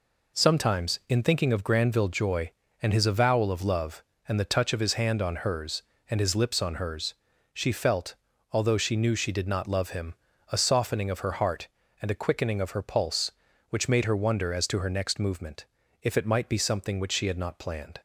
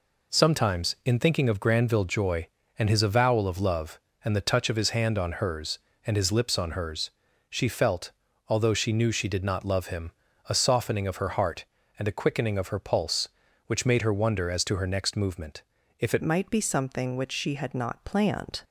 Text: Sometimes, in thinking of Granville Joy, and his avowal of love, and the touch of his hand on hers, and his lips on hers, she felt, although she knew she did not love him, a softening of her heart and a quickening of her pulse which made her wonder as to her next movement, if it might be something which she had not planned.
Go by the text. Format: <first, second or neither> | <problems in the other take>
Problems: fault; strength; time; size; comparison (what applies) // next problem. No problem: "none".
first | changes voice at "might"; from 16.2 s on; 2.4 s long